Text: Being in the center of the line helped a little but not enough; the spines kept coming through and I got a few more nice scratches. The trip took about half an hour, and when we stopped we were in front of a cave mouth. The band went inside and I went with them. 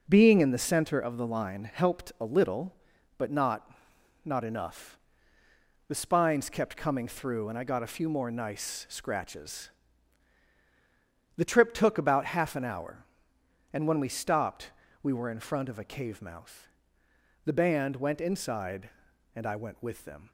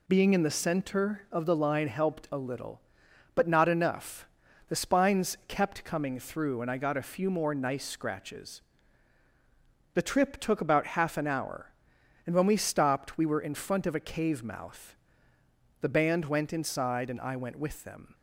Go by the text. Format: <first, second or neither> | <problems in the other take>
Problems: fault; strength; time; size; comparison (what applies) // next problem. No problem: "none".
second | says "not" twice; at 4.2 s // pauses between "stopped" and "we"; slight; at 14.6 s; 0.32 s long